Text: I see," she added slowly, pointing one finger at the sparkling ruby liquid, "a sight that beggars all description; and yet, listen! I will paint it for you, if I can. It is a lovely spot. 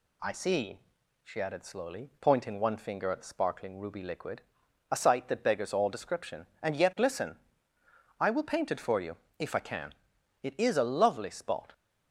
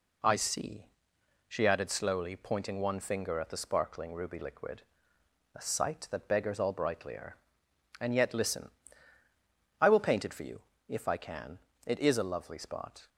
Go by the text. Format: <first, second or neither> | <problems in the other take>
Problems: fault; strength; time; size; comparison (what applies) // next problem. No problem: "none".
first | says "brightlier" for "description"; at 6.7 s